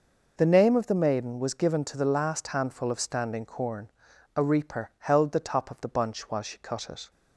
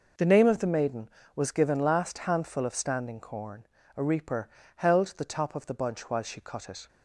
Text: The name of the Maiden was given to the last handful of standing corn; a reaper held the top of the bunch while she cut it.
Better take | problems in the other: first | skips "to the"; at 1.7 s // pauses between "reaper" and "held"; slight; at 4.4 s; 0.28 s long

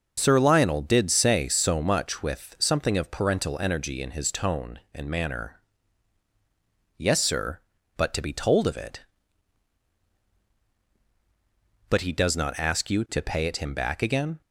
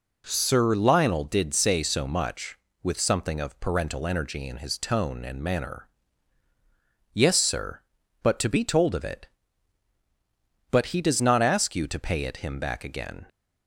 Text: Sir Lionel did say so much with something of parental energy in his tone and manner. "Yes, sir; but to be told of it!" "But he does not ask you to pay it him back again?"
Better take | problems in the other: neither | none

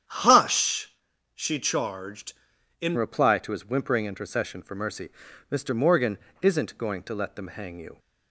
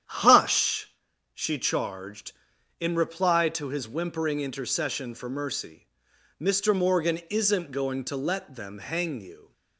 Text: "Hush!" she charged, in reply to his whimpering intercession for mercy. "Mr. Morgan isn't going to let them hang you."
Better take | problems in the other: second | starts louder than the rest; strong; until 1.4 s; 9 dB; strong in the second // changes voice at "reply"; from 2.9 s on; 5.0 s long // pauses between "Morgan" and "isn't"; slight; at 6.1 s; 0.24 s long

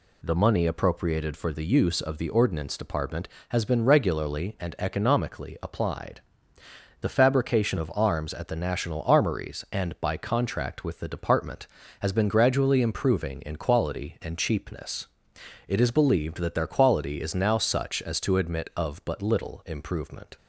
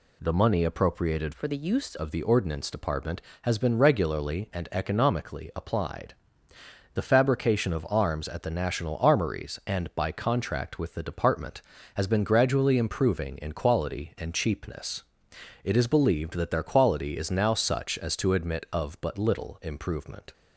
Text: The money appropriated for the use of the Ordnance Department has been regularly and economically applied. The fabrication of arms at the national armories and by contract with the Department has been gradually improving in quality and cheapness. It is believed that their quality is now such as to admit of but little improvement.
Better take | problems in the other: first | changes voice from "for" to "use"; from 1.3 to 1.9 s; 0.6 s long

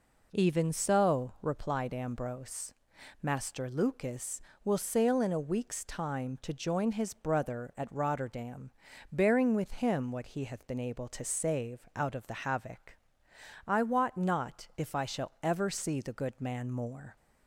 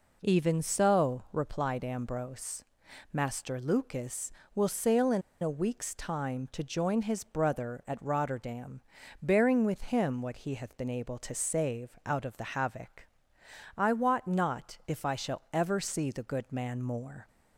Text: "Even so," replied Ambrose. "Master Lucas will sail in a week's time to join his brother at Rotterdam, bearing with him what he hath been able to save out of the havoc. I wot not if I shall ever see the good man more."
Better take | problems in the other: first | pauses between "in" and "a"; slight; at 5.2 s; 0.21 s long

